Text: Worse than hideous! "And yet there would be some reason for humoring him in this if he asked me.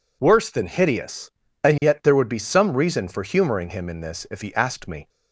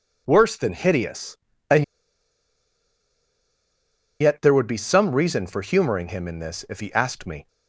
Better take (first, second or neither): first